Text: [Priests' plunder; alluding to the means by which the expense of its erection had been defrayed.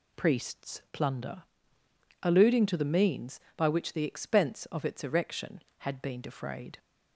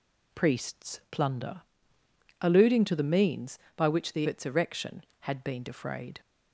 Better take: first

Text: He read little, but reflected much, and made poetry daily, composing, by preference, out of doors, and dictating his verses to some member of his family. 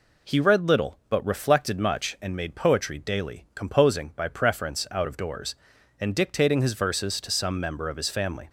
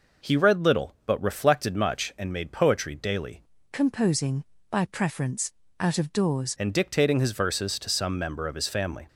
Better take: first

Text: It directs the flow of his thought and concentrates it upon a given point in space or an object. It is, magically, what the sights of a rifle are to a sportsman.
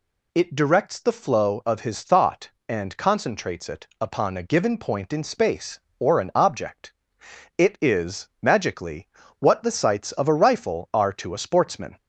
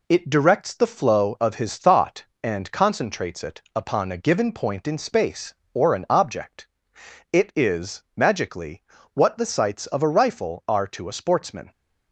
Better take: first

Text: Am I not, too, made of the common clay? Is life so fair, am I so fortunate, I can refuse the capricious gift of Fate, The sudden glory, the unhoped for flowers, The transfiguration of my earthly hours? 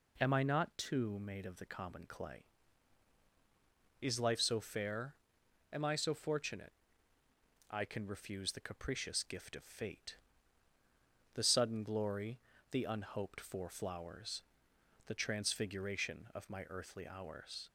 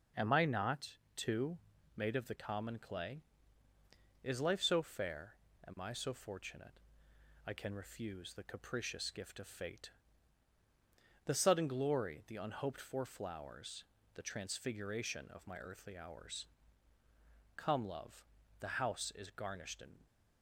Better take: first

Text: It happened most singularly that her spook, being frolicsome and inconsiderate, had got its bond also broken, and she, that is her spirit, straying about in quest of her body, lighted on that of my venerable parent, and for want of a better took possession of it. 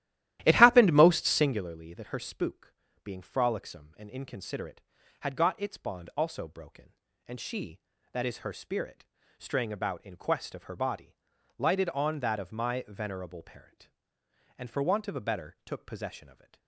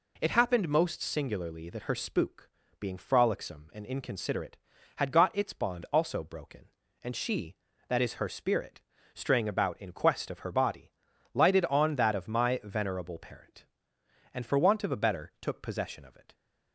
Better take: second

